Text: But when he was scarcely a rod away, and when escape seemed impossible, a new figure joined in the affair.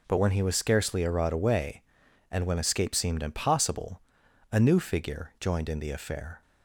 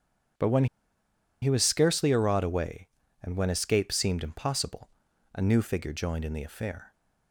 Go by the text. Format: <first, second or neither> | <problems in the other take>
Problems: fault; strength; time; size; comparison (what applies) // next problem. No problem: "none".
first | starts louder than the rest; strong; until 2.1 s; 8.5 dB // pauses between "when" and "he"; noticeable; at 0.6 s; 0.76 s long